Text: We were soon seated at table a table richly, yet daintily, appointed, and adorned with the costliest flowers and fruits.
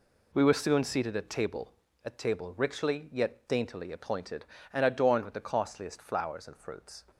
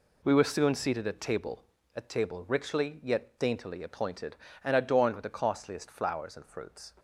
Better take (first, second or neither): neither